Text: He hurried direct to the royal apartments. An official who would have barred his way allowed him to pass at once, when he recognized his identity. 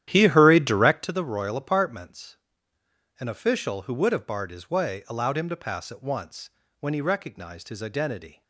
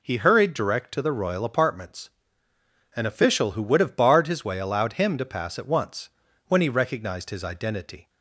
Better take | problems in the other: second | starts louder than the rest; strong; until 1.1 s; 11.5 dB

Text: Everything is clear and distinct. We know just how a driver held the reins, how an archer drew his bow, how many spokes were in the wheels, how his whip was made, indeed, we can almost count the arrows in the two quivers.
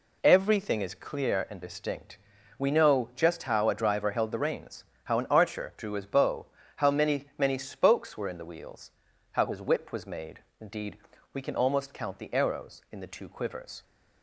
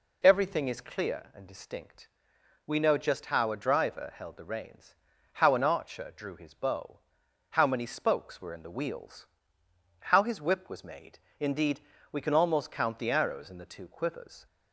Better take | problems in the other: second | says "many" twice; at 7.3 s

